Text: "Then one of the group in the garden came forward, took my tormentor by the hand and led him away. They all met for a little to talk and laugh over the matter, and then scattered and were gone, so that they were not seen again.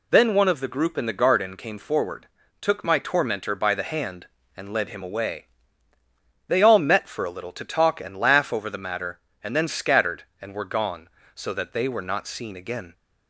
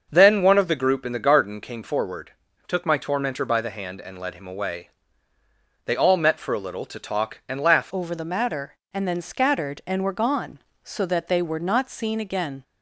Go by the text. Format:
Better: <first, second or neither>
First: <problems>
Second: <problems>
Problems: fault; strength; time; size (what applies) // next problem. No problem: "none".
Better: first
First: none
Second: starts louder than the rest; until 1.1 s; 6 dB // changes voice at "over"; from 7.9 s on; 4.7 s long